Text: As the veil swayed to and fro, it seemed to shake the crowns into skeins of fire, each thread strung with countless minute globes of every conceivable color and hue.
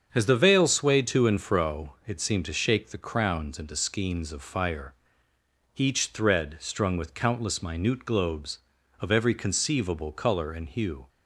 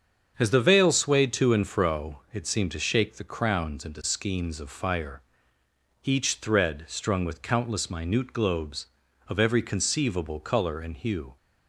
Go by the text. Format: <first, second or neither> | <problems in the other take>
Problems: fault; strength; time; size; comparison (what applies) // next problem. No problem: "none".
neither | starts louder than the rest; strong; the same in both